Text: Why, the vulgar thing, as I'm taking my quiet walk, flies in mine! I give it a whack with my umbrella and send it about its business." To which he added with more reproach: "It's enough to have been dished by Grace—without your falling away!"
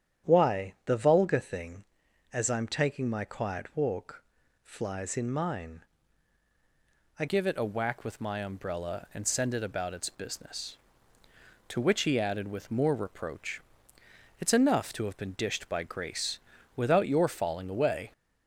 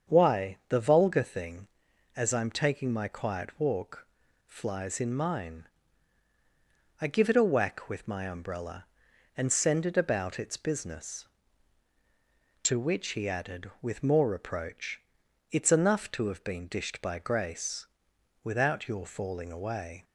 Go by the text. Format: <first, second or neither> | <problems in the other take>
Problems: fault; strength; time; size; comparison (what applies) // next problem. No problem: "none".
second | starts louder than the rest; strong; until 1.3 s; 9.5 dB; strong in the second // changes voice at "give"; from 7.2 s on; 10.9 s long